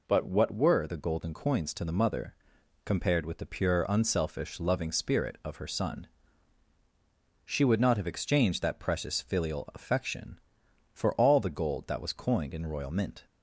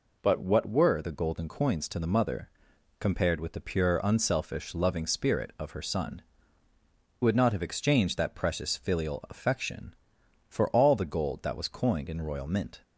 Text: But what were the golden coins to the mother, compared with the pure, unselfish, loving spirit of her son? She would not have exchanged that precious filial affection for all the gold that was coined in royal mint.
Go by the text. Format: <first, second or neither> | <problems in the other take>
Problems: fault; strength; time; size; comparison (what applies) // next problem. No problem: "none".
first | skips "She"; at 6.7 s